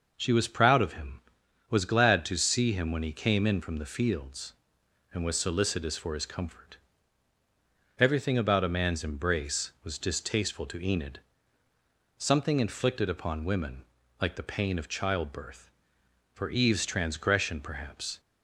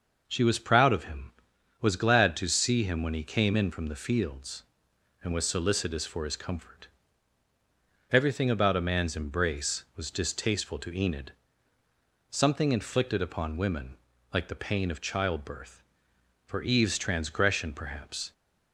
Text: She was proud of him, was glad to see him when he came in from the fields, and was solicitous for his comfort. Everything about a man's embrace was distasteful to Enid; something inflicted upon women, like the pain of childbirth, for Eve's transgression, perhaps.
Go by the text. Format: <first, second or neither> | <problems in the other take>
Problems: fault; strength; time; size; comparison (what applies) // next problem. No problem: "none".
neither | none